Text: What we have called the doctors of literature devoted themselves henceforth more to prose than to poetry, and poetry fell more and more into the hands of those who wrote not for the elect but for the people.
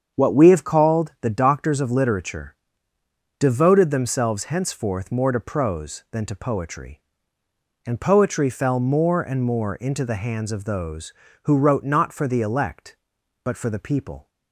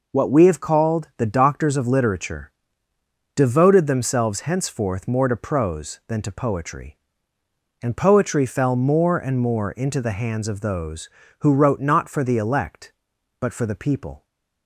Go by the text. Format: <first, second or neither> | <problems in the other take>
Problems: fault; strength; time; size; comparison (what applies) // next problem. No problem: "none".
second | starts louder than the rest; strong; until 1.2 s; 7.5 dB // pauses between "literature" and "devoted"; noticeable; at 2.5 s; 0.84 s long; noticeable in the second